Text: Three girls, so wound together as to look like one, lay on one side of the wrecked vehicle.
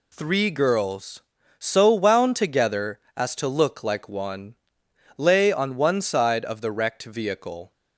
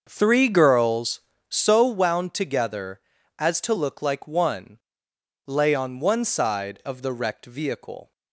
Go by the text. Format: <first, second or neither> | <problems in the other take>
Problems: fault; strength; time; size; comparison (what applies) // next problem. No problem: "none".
first | starts louder than the rest; until 1.9 s; 6.5 dB